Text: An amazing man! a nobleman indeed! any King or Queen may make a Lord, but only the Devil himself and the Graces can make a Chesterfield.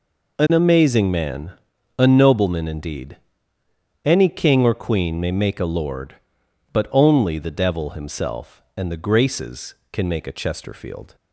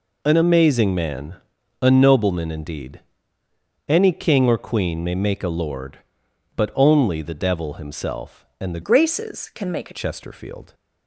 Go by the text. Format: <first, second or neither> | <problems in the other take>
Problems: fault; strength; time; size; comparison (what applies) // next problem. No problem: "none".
first | changes voice from "Graces" to "a"; from 8.8 to 9.9 s; 1.1 s long